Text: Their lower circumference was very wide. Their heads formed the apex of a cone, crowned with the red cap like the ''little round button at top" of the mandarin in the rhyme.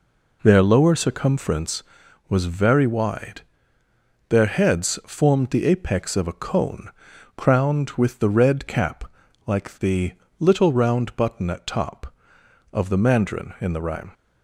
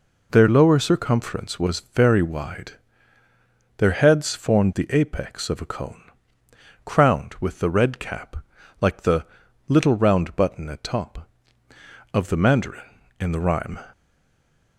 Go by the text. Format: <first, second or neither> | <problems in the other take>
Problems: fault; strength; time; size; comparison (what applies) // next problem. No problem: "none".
first | pauses between "cap" and "like"; at 8.3 s; 0.42 s long; also in the first // pauses between "the" and "little"; at 9.2 s; 0.42 s long; slight in the first // stays silent after the last word; slight; from 13.9 s on; 0.8 s long